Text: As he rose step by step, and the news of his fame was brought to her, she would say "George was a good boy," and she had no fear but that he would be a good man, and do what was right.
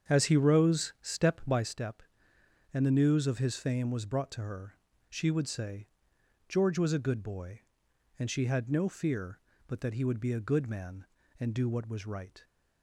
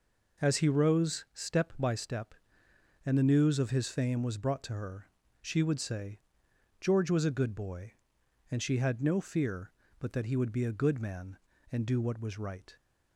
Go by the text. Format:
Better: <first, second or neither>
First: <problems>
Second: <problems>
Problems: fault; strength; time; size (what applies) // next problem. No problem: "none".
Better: second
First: starts louder than the rest; strong; until 1.8 s; 7.5 dB // pauses between "say" and "George"; noticeable; at 5.8 s; 0.60 s long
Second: pauses between "say" and "George"; noticeable; at 6.1 s; 0.60 s long